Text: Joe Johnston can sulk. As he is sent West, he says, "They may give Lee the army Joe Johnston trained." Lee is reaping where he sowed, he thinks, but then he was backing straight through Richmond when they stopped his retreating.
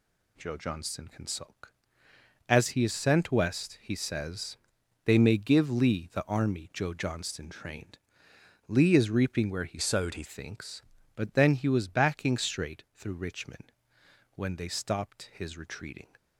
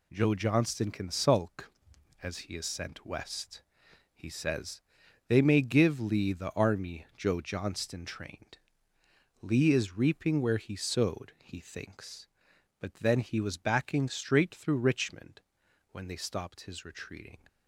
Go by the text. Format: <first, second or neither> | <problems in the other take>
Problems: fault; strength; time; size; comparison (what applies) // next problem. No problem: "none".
second | changes voice from "sowed" to "he"; from 9.7 to 10.2 s; 0.5 s long // pauses between "Richmond" and "when"; noticeable; at 13.7 s; 0.64 s long; noticeable in the second